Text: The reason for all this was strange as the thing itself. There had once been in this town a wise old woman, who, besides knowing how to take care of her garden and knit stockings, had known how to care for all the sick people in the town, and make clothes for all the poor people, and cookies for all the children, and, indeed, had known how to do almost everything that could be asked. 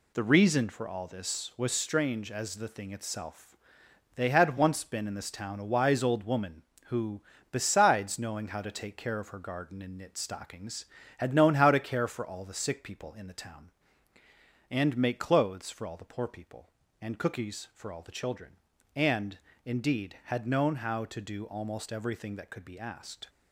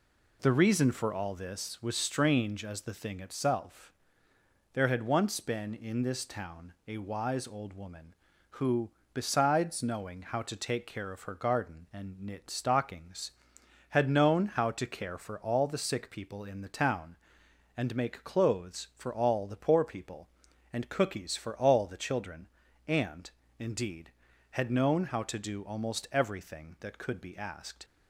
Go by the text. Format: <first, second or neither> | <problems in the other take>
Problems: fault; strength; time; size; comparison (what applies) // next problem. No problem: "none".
second | says "They" for "There"; at 4.1 s